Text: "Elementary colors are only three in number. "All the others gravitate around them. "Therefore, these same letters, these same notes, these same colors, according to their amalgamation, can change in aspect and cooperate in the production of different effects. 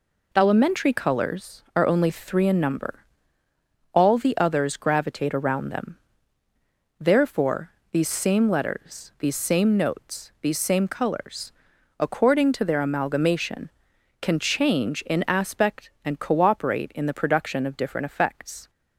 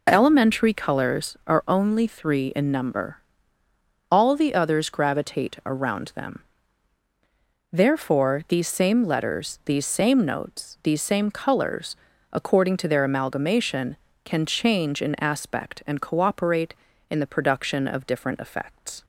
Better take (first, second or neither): neither